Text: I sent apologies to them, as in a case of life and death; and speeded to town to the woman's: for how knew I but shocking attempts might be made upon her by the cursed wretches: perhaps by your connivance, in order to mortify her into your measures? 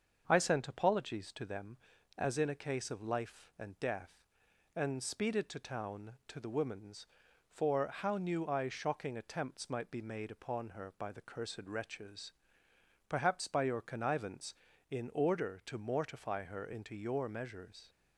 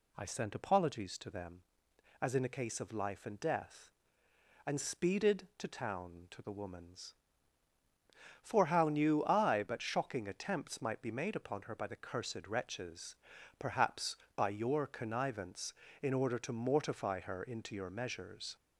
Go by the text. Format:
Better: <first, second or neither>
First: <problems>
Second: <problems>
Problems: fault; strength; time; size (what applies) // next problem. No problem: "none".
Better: second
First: starts louder than the rest; until 1.2 s; 6.5 dB // skips "but"; at 8.6 s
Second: none